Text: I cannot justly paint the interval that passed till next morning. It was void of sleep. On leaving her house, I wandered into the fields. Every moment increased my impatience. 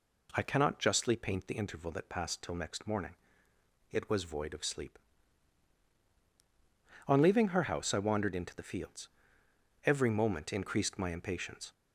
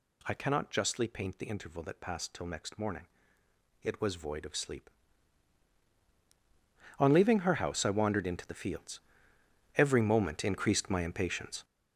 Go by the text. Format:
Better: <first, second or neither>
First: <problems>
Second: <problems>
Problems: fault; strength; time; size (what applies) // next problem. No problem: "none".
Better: first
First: none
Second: gets louder; strong; throughout; 8 dB